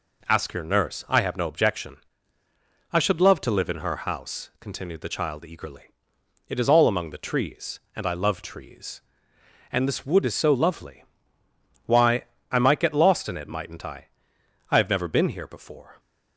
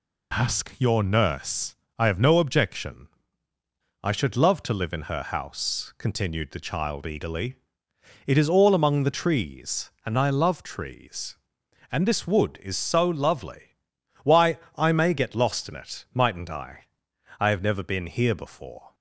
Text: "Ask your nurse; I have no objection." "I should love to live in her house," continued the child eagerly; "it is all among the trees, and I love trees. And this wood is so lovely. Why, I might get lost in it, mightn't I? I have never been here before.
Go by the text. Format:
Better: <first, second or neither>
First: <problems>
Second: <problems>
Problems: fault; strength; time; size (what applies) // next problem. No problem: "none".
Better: first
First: none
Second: says "may" for "might"; at 14.9 s